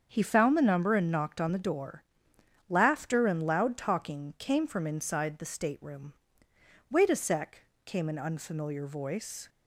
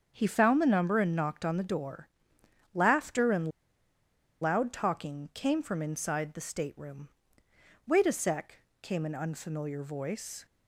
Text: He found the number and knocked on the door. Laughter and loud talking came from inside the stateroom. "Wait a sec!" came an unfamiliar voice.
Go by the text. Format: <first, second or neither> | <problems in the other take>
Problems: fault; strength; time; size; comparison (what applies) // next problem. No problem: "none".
first | starts louder than the rest; until 1.1 s; 7 dB; also in the first // pauses between "and" and "loud"; noticeable; at 3.5 s; 0.90 s long